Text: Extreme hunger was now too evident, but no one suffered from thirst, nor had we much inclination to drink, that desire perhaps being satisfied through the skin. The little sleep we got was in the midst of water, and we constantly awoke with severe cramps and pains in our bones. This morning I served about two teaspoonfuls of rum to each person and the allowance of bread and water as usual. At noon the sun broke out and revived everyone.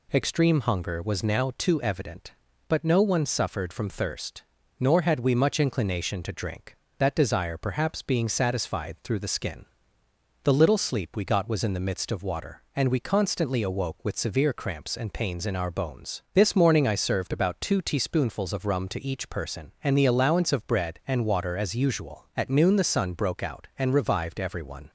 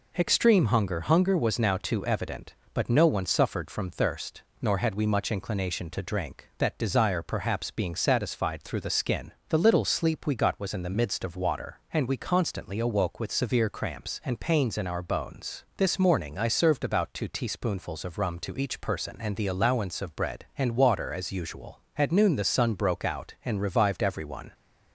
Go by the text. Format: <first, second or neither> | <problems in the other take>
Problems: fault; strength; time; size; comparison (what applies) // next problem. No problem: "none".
first | says "hunger" twice; at 1.0 s